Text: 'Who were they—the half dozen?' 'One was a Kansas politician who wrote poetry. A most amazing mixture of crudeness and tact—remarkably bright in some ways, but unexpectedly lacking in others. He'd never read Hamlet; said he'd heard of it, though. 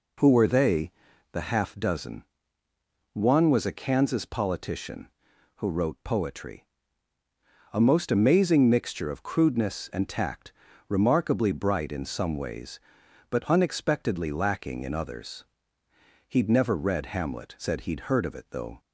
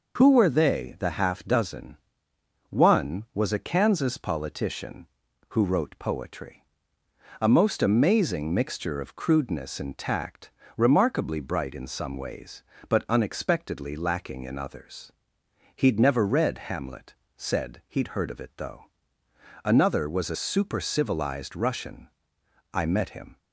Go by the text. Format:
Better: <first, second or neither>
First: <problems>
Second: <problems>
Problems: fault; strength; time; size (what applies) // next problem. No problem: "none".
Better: first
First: none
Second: goes on to say "Another was a super civilized Russian I met him"; strong; from 19.6 s on; 3.7 s long